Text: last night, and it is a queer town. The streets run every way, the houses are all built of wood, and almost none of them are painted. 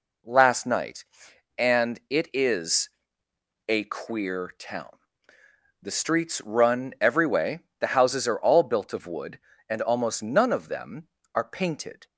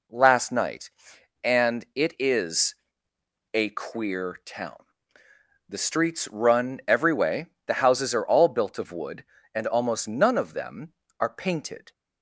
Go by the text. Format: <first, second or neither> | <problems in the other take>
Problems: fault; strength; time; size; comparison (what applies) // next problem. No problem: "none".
neither | pauses between "is" and "a"; noticeable; the same in both